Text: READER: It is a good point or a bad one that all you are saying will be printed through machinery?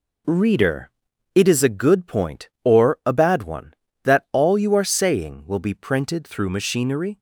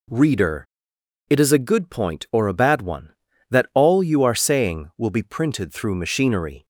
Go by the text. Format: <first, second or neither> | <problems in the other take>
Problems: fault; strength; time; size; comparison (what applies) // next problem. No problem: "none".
neither | none